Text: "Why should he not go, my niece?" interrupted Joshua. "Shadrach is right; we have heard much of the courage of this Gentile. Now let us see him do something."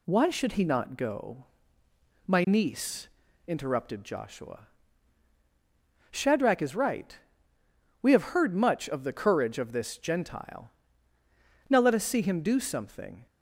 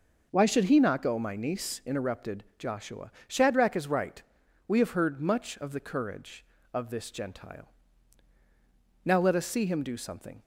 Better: neither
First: none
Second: none

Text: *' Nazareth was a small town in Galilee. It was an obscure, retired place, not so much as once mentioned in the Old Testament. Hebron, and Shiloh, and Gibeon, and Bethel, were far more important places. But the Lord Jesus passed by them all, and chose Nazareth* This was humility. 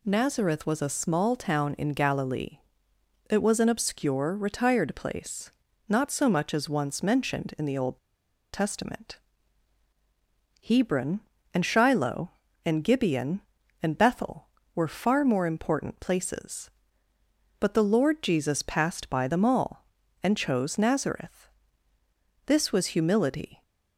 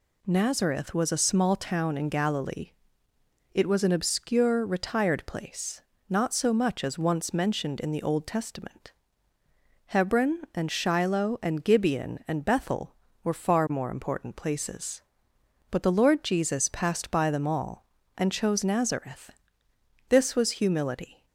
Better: second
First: pauses between "Old" and "Testament"; noticeable; at 7.9 s; 0.54 s long // pauses between "Nazareth" and "This"; noticeable; at 21.4 s; 0.98 s long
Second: pauses between "Nazareth" and "This"; noticeable; at 19.2 s; 0.78 s long

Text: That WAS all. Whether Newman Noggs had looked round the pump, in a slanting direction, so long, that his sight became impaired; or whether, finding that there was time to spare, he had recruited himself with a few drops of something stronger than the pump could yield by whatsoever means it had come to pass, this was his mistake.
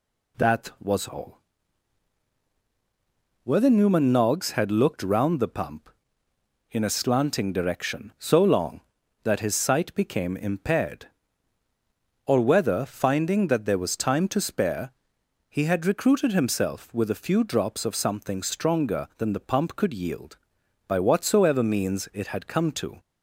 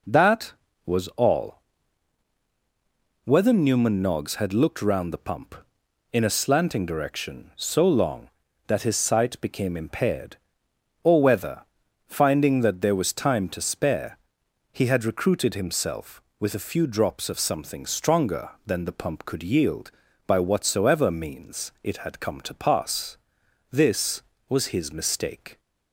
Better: second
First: stops before "pass this was his mistake"; at 22.9 s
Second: none

